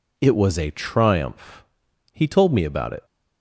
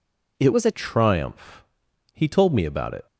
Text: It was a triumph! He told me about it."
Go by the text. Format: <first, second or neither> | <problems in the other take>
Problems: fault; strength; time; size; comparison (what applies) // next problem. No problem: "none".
first | changes voice from "was" to "a"; from 0.5 to 0.7 s; 0.2 s long